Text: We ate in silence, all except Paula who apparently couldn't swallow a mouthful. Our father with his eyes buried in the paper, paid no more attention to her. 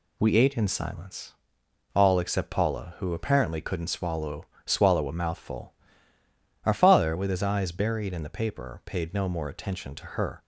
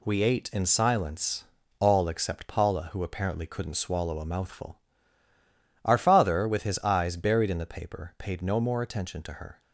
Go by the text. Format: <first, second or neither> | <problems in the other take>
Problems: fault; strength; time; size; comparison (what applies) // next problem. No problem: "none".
second | says "swallow" twice; at 4.6 s